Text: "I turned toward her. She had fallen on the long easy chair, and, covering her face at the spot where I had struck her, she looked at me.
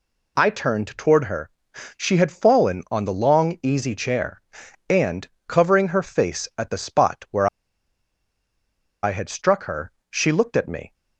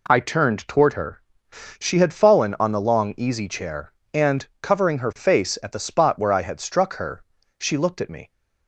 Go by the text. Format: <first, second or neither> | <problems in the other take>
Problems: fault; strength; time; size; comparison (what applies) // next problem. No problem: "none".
second | pauses between "where" and "I"; strong; at 7.4 s; 1.5 s long